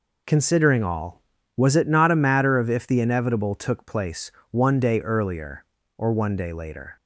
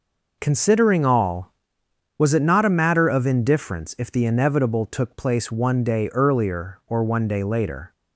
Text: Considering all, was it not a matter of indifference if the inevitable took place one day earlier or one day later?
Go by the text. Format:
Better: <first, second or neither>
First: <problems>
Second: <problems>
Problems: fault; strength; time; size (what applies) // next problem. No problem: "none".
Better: second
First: skips "indifference"; at 2.6 s // pauses between "place" and "one"; slight; at 4.2 s; 0.20 s long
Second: none